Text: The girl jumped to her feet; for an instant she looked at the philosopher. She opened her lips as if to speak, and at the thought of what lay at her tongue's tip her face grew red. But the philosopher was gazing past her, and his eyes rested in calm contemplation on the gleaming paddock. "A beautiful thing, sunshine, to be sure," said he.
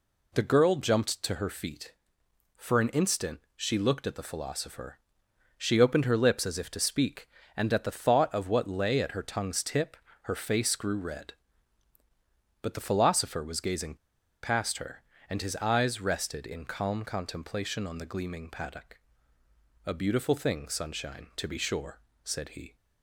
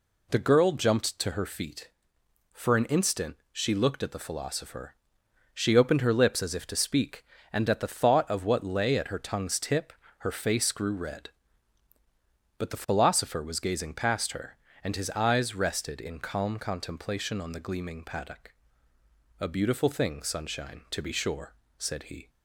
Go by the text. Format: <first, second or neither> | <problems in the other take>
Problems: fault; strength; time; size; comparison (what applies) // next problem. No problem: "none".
second | pauses between "tip" and "her"; slight; at 9.9 s; 0.28 s long; slight in the second // pauses between "gazing" and "past"; noticeable; at 13.9 s; 0.46 s long